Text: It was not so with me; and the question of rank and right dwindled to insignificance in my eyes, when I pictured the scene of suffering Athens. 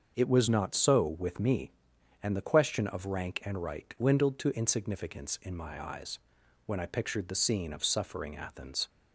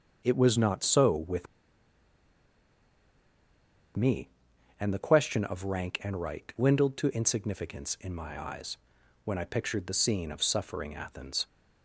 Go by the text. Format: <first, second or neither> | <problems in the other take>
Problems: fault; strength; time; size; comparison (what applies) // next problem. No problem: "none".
first | starts louder than the rest; until 1.2 s; 6 dB; also in the first // pauses between "with" and "me"; strong; at 1.4 s; 2.4 s long